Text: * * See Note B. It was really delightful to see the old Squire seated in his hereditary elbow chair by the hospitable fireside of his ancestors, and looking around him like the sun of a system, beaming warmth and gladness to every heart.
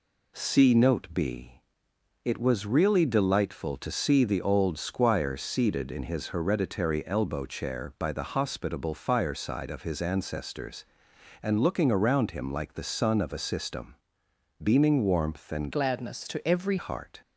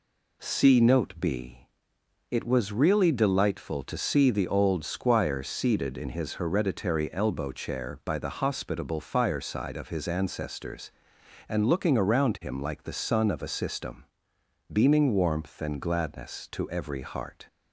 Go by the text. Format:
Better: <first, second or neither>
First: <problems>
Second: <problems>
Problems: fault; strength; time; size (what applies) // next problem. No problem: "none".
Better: second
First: changes voice from "gladness" to "every"; from 15.7 to 16.7 s; 1.0 s long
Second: none